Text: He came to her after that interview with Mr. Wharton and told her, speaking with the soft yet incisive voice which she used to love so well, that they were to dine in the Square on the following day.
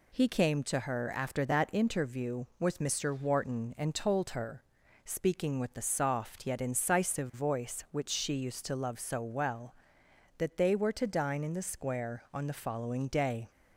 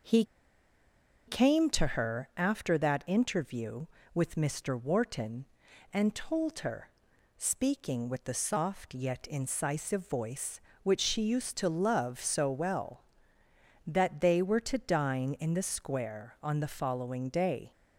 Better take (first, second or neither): first